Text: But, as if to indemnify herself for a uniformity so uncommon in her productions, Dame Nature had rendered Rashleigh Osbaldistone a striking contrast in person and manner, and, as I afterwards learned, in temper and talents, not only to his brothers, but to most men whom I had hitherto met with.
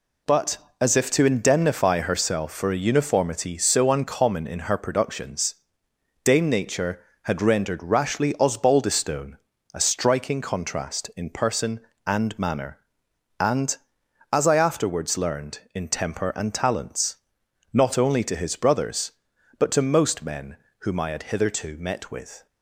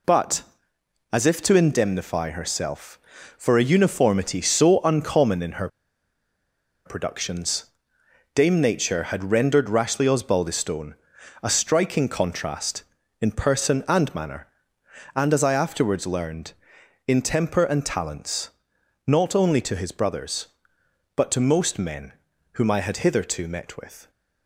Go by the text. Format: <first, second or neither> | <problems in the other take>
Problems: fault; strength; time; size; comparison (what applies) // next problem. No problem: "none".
first | pauses between "her" and "productions"; at 5.6 s; 1.1 s long // pauses between "Osbaldistone" and "a"; noticeable; at 10.9 s; 0.48 s long; slight in the first // pauses between "men" and "whom"; at 22.1 s; 0.40 s long; slight in the first